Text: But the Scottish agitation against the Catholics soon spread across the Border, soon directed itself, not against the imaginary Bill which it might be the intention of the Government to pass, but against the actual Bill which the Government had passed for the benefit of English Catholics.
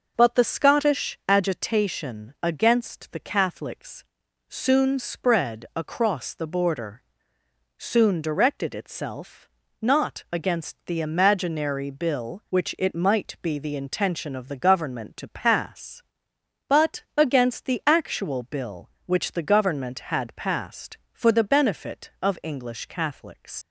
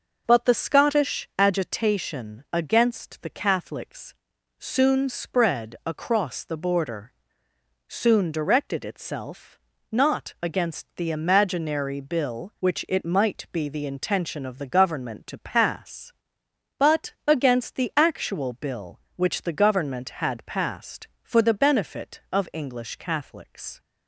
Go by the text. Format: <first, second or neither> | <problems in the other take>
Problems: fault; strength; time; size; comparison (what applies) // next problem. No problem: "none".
second | pauses between "Catholics" and "soon"; at 4.0 s; 0.44 s long; also in the second // leaves "Catholics" unfinished; at 23.6 s; 80 ms